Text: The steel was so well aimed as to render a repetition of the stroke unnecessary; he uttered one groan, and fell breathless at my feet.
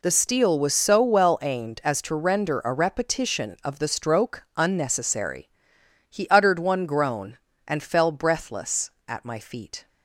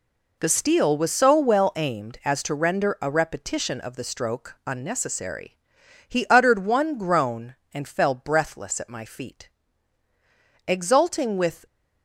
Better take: first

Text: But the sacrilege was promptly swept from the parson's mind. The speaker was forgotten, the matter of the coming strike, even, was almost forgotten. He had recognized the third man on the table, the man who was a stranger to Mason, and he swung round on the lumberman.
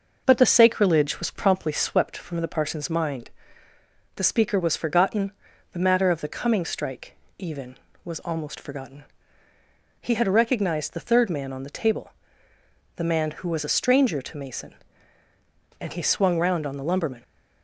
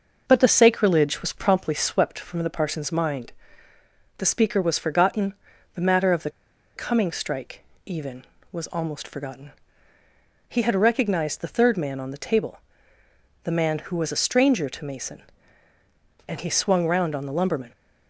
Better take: first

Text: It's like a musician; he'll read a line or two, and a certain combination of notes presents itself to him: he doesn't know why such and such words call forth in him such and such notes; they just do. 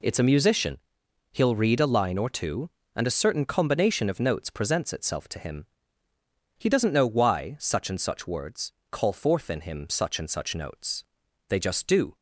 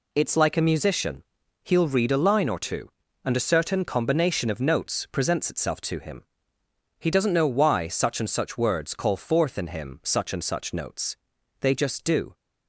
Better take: second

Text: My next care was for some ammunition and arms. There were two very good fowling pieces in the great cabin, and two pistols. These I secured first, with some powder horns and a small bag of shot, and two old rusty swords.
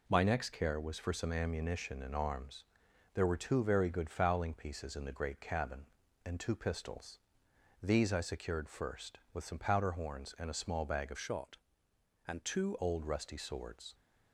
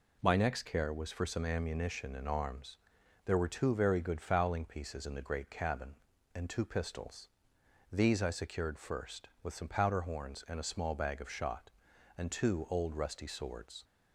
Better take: second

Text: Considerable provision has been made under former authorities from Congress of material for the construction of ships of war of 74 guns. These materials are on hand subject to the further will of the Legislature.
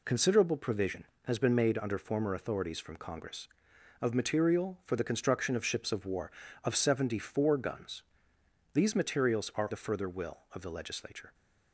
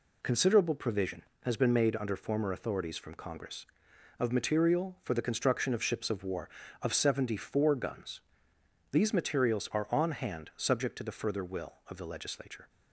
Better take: second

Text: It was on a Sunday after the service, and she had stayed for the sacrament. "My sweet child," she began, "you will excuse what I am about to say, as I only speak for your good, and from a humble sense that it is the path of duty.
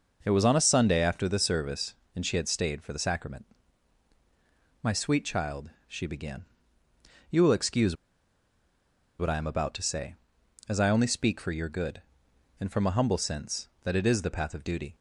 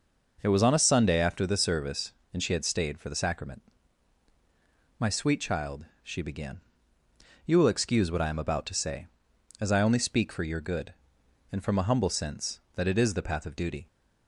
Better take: second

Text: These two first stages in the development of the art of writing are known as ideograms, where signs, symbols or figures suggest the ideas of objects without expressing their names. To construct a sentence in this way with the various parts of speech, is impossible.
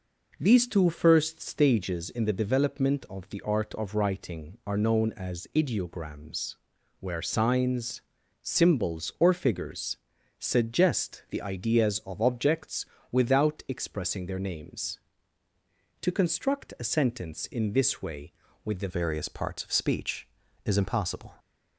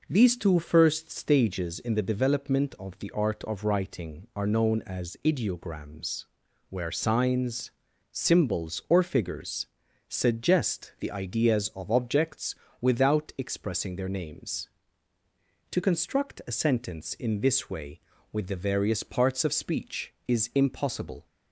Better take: second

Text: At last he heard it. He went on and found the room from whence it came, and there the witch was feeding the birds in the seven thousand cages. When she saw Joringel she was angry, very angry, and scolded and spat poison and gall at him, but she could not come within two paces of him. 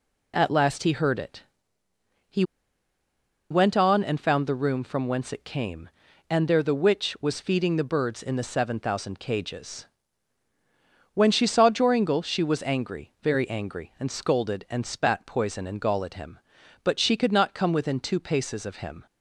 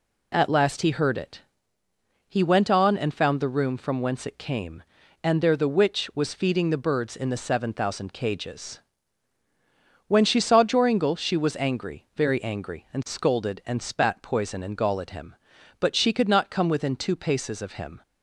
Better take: second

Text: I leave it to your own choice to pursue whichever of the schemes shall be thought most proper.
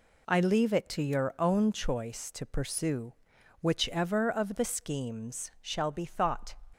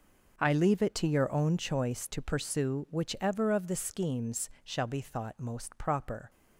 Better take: second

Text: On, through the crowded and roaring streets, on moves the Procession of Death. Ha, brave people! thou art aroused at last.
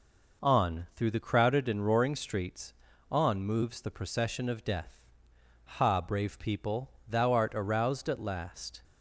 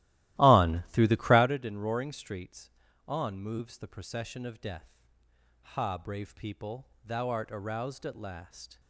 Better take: first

